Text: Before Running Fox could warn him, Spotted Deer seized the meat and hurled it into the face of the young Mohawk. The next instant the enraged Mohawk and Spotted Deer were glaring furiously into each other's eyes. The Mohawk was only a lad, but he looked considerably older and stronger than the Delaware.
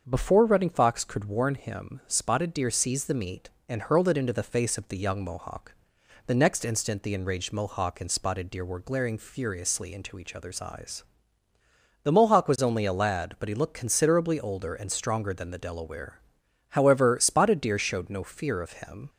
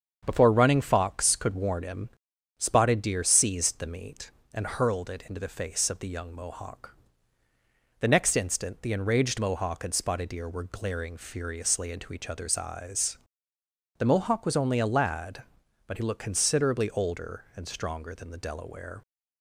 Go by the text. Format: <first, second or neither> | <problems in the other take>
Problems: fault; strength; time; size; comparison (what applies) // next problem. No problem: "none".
second | starts louder than the rest; until 1.0 s; 6.5 dB; strong in the second // goes on to say "However Spotted Deer showed no fear of him"; strong; from 16.7 s on; 2.3 s long